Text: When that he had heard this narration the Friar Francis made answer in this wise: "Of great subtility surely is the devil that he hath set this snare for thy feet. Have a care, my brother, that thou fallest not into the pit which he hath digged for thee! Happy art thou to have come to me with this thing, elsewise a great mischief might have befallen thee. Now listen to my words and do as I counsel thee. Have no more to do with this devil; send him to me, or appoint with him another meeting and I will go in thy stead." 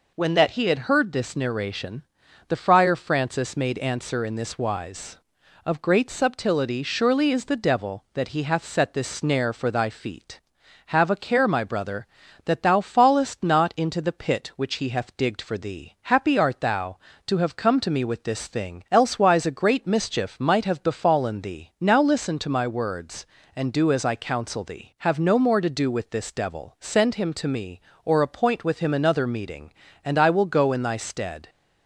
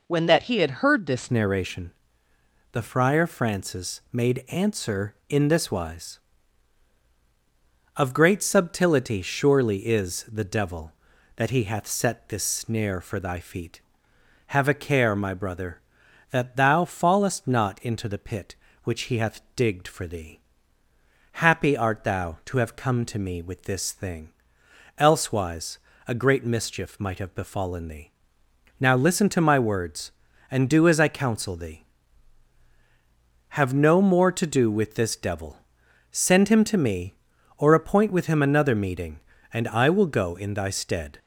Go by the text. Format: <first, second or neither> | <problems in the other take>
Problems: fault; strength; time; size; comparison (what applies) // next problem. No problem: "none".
first | changes voice at "narration"; from 1.3 s on; 39.8 s long // pauses between "narration" and "the"; noticeable; at 1.9 s; 0.80 s long; noticeable in the first // pauses between "hath" and "digged"; slight; at 19.4 s; 0.16 s long // pauses between "elsewise" and "a"; slight; at 25.7 s; 0.28 s long